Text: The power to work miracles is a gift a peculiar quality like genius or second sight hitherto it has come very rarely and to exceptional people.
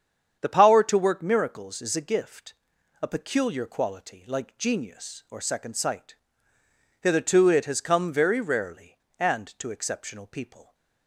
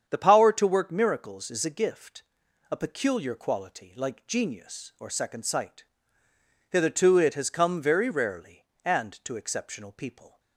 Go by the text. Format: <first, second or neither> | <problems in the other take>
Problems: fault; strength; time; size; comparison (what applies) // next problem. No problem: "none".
neither | starts louder than the rest; strong; the same in both // pauses between "gift" and "a"; noticeable; the same in both // pauses between "sight" and "hitherto"; noticeable; the same in both